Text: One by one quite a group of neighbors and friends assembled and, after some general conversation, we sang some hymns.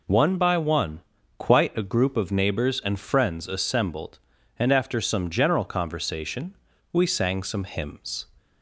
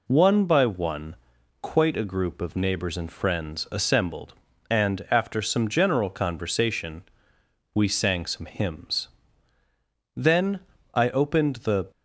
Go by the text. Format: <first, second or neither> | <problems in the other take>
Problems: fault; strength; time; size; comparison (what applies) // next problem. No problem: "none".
first | pauses between "one" and "quite"; at 1.1 s; 0.44 s long; also in the first // goes on to say "Then I opened the"; strong; from 10.1 s on; 1.7 s long